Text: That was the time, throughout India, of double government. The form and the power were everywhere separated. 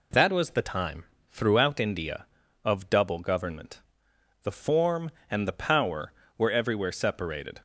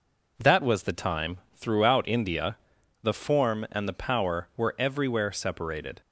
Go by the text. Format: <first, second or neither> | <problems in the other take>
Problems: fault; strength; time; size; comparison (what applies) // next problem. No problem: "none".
first | skips "of double government"; at 2.8 s